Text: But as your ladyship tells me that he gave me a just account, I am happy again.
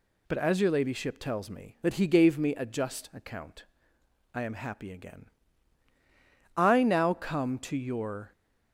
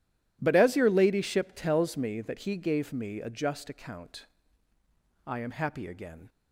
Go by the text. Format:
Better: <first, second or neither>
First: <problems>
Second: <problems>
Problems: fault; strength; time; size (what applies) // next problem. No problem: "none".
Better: second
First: goes on to say "I now come to your"; strong; from 6.5 s on; 1.7 s long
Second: none